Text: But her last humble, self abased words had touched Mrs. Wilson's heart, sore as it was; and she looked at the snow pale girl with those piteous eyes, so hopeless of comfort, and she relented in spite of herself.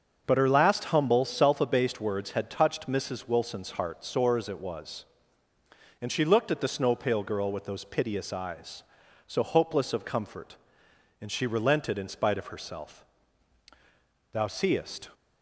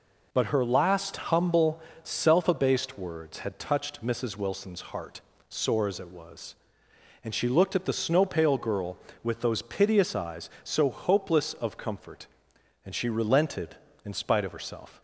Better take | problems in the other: second | starts louder than the rest; until 1.2 s; 6.5 dB // goes on to say "Thou seest"; noticeable; from 14.3 s on; 0.78 s long

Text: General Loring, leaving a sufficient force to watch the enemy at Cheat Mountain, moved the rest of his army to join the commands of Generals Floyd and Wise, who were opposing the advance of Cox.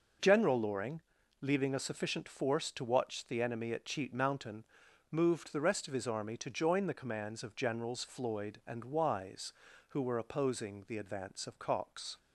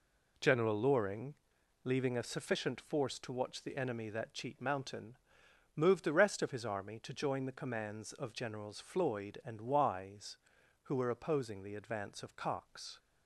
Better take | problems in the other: first | says "that" for "at"; at 4.1 s

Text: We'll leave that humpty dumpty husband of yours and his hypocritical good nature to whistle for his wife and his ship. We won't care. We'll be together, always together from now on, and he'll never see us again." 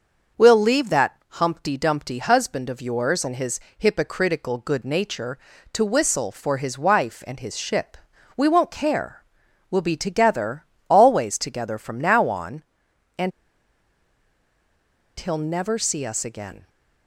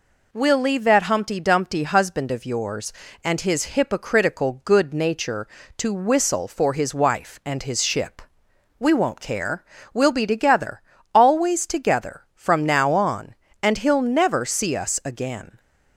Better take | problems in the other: second | starts louder than the rest; noticeable; until 1.4 s; 6 dB // pauses between "his" and "hypocritical"; slight; at 3.5 s; 0.20 s long // pauses between "and" and "he'll"; strong; at 13.3 s; 1.8 s long

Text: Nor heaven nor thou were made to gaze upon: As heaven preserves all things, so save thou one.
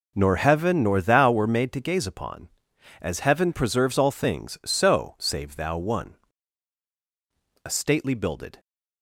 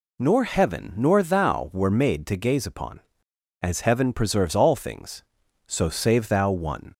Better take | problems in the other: second | goes on to say "A stately builded"; noticeable; from 7.6 s on; 0.94 s long

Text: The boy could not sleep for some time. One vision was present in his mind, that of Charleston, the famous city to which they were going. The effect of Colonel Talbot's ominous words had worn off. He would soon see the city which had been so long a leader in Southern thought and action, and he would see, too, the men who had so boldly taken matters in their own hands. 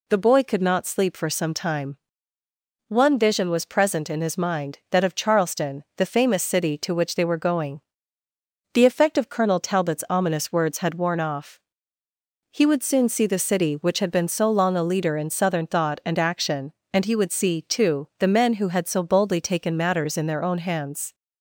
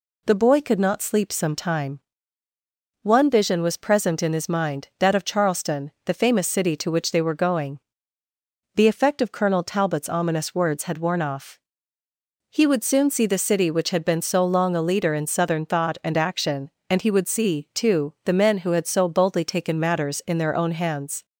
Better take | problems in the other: first | skips "for"; at 1.3 s

